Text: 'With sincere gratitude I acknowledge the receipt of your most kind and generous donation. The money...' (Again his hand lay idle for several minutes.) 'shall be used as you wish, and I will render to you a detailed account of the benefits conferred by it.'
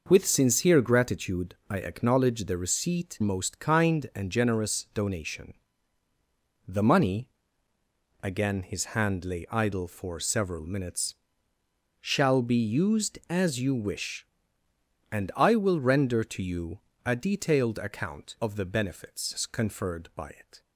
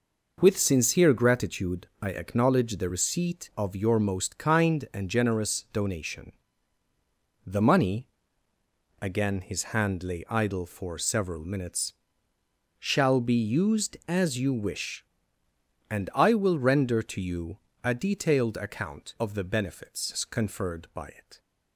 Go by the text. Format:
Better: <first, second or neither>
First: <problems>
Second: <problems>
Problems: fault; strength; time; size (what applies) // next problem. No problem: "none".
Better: second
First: skips "of your"; at 3.1 s // pauses between "you" and "a"; slight; at 16.7 s; 0.26 s long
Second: pauses between "you" and "a"; slight; at 17.5 s; 0.26 s long